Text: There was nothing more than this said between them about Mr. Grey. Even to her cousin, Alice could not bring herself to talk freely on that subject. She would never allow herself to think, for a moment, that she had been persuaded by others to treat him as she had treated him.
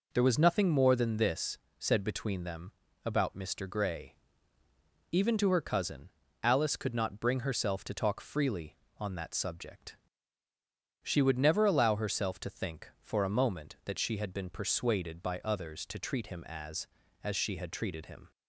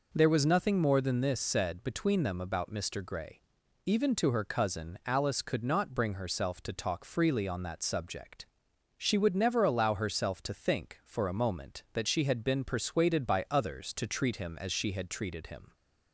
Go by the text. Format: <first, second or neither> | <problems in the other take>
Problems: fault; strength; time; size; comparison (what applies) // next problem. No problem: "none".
second | pauses between "this" and "said"; slight; at 1.5 s; 0.22 s long // pauses between "them" and "about"; slight; at 2.7 s; 0.32 s long // says "as" twice; at 17.2 s